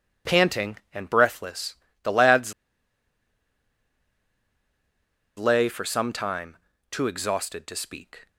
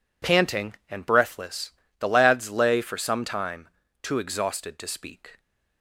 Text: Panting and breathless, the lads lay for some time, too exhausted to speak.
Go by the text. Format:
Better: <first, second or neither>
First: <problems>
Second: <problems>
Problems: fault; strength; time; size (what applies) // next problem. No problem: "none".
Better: second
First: pauses between "lads" and "lay"; strong; at 2.5 s; 2.8 s long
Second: none